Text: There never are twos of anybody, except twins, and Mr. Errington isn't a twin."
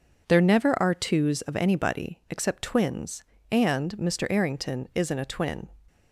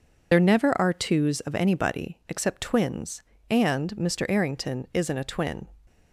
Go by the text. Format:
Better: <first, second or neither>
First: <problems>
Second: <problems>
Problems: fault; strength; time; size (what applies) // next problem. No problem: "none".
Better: first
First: none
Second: loses the start of "There"; at 0.3 s; 60 ms